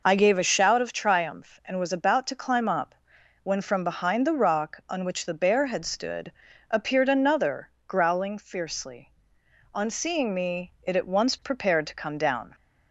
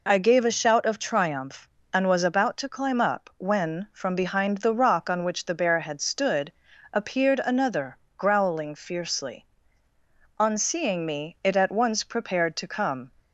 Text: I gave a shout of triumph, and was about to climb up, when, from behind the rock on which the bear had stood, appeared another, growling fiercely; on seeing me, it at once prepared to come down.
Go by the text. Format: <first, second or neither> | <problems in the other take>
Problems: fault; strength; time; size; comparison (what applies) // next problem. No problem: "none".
first | stops before "down"; at 13.1 s